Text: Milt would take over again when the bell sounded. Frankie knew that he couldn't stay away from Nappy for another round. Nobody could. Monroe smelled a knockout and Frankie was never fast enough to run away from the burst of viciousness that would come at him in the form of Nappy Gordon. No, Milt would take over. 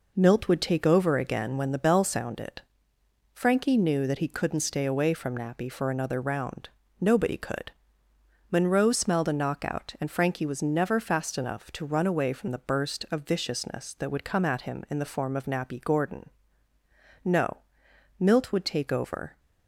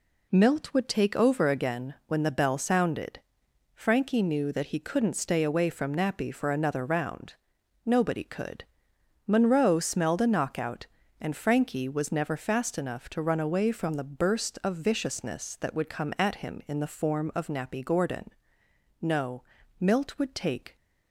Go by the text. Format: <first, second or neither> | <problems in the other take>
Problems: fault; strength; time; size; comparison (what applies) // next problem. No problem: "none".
first | stops before "over"; at 20.7 s